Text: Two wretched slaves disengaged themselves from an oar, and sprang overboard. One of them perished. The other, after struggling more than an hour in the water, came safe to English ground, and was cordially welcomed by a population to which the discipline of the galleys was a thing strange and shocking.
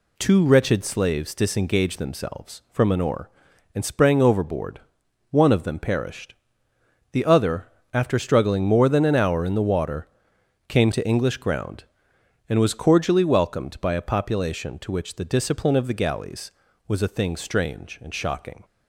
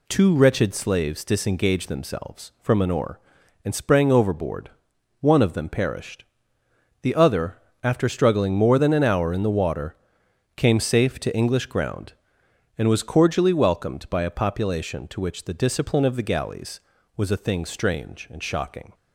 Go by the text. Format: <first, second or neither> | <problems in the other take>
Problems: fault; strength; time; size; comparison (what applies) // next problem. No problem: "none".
second | skips "safe"; at 10.9 s